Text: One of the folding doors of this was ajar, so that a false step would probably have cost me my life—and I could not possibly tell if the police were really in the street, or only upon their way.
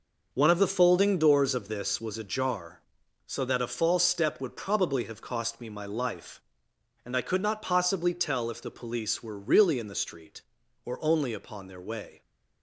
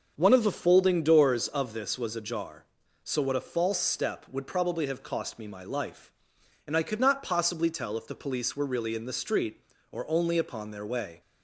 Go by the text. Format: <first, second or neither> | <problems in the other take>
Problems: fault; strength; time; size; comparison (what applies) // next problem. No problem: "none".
first | starts louder than the rest; until 1.1 s; 6.5 dB // says "what" for "that"; at 3.2 s